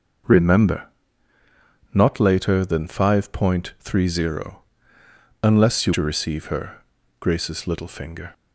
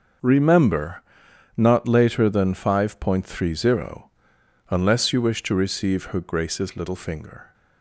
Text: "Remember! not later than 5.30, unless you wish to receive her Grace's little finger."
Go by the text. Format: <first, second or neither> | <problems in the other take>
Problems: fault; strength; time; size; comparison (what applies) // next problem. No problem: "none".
second | starts louder than the rest; noticeable; until 2.3 s; 6 dB; also in the second // skips "wish"; at 5.9 s // pauses between "her" and "Grace's"; at 6.8 s; 0.38 s long